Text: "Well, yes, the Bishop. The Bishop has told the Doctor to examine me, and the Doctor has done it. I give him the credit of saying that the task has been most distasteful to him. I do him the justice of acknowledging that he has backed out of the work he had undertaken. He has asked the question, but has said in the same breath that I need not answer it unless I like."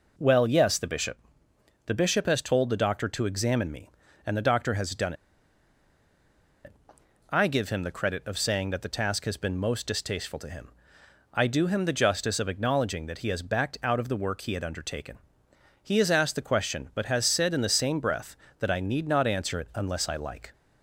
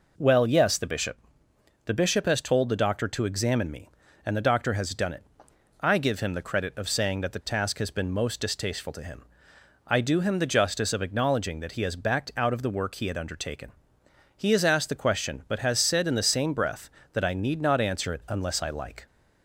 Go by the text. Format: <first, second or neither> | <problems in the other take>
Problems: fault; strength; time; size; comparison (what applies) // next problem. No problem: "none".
second | pauses between "done" and "it"; strong; at 5.1 s; 1.5 s long